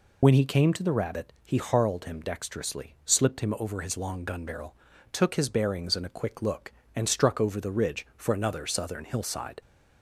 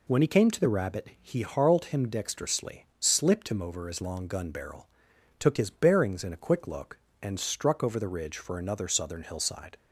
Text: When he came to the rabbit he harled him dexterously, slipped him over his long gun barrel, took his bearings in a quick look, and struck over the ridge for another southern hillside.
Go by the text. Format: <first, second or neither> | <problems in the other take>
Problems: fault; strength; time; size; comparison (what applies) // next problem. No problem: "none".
second | loses the start of "When"; at 0.2 s; 35 ms